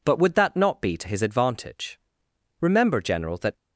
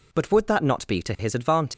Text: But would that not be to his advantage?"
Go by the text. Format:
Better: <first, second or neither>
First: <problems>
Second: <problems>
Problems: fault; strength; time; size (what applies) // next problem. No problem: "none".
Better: second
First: goes on to say "Remember General that"; noticeable; from 2.6 s on; 0.96 s long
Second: none